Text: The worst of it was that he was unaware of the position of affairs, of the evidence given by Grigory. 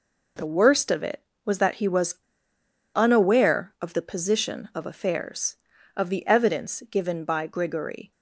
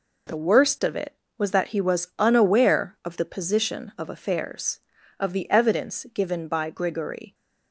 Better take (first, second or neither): second